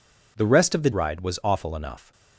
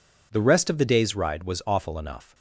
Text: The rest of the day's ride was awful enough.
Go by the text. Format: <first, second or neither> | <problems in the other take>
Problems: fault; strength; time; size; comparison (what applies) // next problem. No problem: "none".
second | skips "day's"; at 0.9 s